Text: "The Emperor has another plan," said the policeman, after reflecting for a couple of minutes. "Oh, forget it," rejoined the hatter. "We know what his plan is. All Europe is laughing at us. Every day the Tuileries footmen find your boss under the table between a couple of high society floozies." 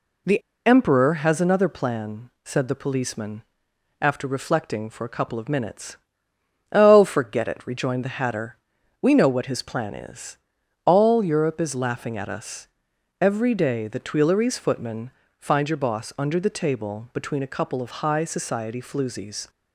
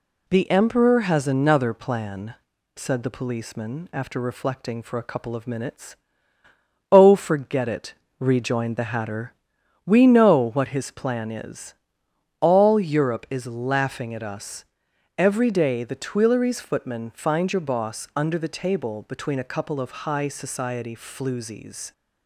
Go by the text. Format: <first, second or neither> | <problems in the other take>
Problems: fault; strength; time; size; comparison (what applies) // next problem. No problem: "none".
second | pauses between "The" and "Emperor"; slight; at 0.4 s; 0.24 s long // pauses between "footmen" and "find"; slight; at 15.1 s; 0.26 s long